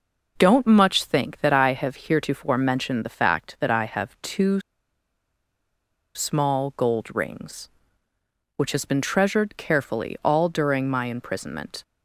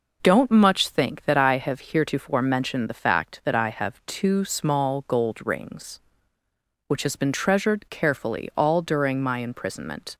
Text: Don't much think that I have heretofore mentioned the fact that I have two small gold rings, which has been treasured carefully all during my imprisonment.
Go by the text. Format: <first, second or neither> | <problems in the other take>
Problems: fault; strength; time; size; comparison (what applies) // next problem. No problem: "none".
second | pauses between "two" and "small"; strong; at 4.6 s; 1.5 s long